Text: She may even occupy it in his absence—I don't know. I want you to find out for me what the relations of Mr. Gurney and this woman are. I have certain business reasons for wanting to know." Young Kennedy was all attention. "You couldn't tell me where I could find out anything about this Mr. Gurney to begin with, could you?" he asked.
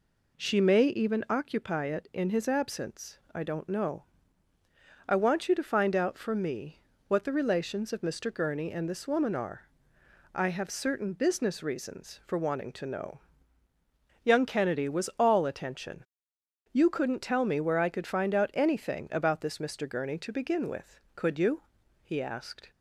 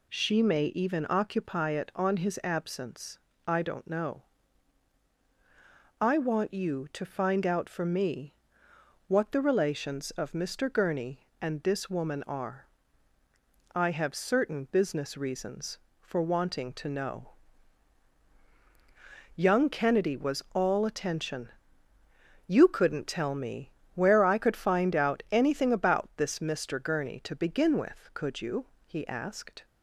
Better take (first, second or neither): first